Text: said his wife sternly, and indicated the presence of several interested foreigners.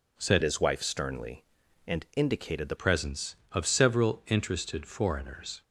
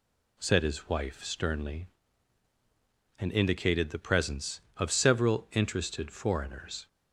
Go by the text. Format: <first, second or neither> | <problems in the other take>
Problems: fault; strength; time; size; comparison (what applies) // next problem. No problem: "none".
second | changes voice from "his" to "the"; from 0.4 to 2.7 s; 2.3 s long